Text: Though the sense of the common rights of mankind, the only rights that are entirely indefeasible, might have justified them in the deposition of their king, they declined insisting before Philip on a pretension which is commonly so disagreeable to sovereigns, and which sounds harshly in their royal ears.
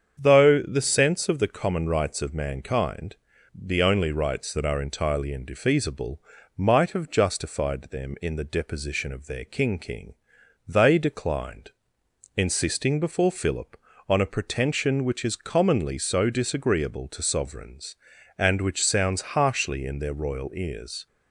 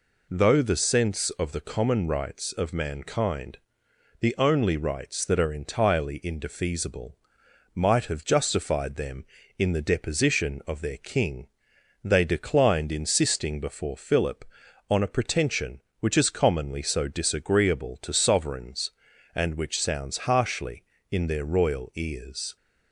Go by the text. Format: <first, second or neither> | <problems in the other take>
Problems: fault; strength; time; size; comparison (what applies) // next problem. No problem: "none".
second | starts louder than the rest; strong; until 1.2 s; 7.5 dB // says "king" twice; at 9.7 s // pauses between "declined" and "insisting"; noticeable; at 11.7 s; 0.66 s long